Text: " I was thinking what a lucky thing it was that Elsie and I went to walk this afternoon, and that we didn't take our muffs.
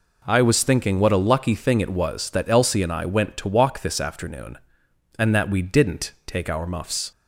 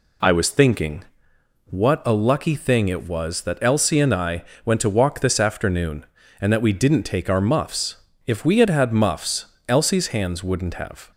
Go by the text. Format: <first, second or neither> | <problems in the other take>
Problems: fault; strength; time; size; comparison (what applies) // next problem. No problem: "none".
first | pauses between "thinking" and "what"; noticeable; at 1.0 s; 0.62 s long // pauses between "I" and "went"; slight; at 4.4 s; 0.22 s long // goes on to say "If we had had muffs Elsie's hands wouldn't have"; strong; from 8.2 s on; 2.8 s long